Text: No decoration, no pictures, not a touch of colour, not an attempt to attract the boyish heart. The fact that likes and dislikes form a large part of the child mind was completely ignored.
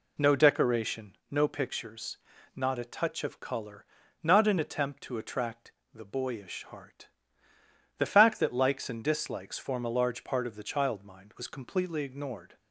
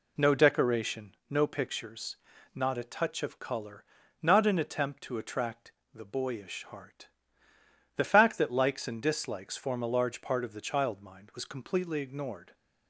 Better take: neither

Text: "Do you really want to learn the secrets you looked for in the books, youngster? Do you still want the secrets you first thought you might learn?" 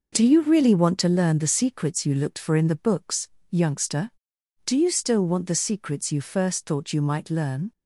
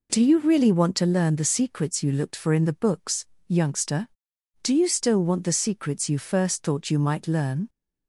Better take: second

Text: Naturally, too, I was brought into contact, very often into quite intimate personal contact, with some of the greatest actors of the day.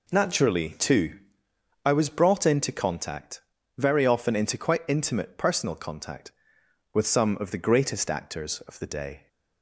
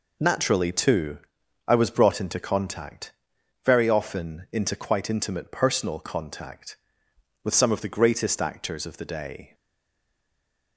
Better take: first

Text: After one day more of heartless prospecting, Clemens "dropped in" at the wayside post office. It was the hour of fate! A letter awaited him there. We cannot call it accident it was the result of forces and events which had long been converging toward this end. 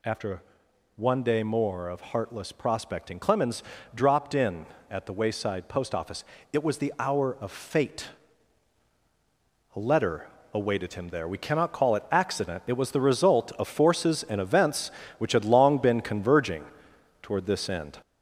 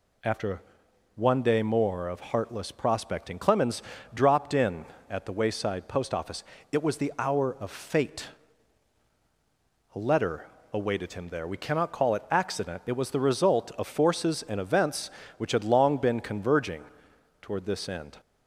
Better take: second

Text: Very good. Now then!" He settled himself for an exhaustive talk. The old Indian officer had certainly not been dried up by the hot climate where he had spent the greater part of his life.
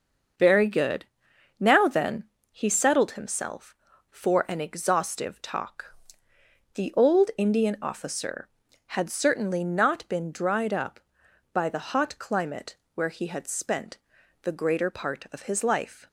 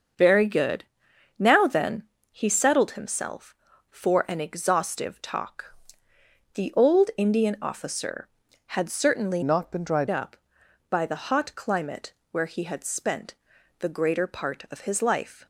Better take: first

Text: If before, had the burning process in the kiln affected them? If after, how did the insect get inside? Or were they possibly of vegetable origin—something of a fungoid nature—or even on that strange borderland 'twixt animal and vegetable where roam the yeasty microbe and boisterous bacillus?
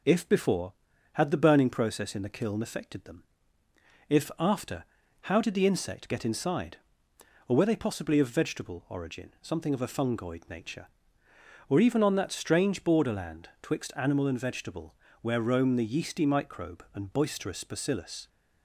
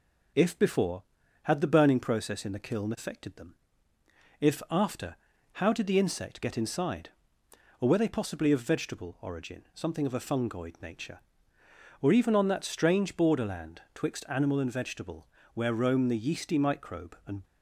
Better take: first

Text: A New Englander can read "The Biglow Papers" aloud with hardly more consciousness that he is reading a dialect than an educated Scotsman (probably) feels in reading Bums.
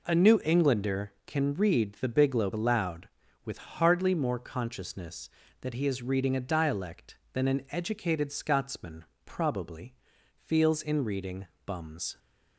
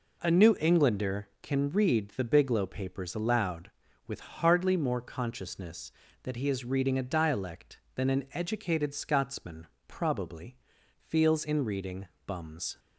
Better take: second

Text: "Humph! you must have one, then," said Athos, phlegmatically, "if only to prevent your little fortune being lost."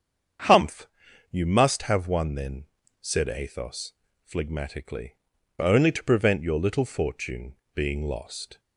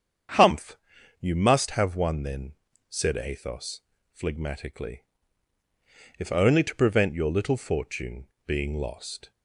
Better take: second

